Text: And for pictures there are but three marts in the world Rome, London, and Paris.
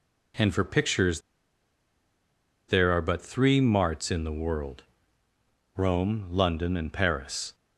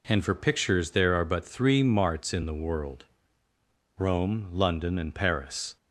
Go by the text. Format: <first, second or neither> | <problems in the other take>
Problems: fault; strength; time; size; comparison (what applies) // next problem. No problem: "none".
second | pauses between "pictures" and "there"; strong; at 1.2 s; 1.4 s long // pauses between "world" and "Rome"; noticeable; at 4.8 s; 0.92 s long; noticeable in the second